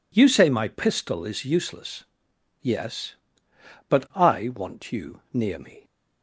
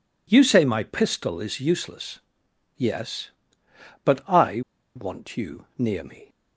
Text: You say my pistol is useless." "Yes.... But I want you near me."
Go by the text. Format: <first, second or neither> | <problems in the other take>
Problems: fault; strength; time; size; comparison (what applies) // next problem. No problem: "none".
first | pauses between "I" and "want"; slight; at 4.6 s; 0.35 s long